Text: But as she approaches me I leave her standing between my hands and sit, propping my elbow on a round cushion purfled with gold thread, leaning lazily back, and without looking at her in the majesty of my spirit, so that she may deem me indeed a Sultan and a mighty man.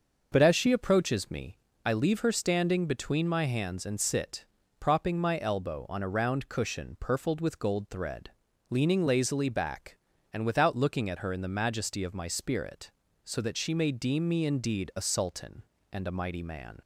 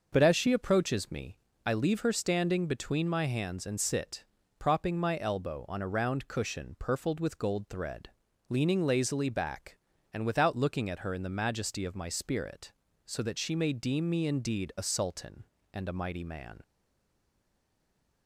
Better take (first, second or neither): first